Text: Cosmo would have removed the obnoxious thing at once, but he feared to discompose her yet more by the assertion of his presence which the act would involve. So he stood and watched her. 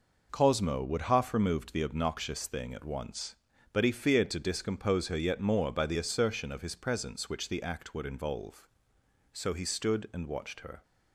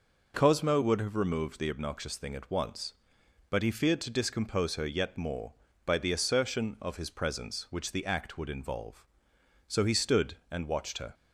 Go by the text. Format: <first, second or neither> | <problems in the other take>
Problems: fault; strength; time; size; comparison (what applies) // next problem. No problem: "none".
second | says "half" for "have"; at 1.0 s